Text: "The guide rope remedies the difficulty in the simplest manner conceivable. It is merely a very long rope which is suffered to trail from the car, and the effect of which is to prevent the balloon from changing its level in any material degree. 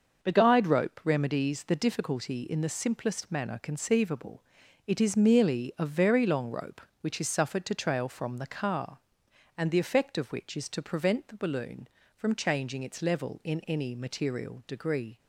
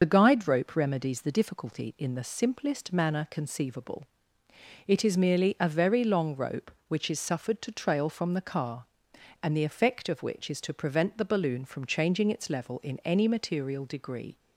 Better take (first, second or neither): first